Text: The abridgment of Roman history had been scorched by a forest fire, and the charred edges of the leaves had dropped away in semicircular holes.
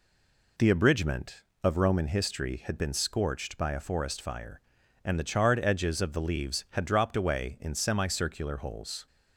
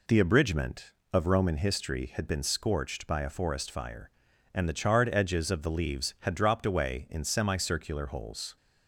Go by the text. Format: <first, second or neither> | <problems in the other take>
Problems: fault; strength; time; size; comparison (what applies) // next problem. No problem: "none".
second | stays silent before the first word; slight; until 0.5 s; 0.5 s long